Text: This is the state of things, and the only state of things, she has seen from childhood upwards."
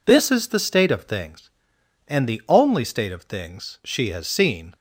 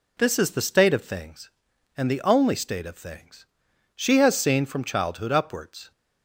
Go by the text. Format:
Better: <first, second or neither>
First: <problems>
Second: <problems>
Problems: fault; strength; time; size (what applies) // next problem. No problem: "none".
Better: second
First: stops before "from childhood upwards"; at 4.7 s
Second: none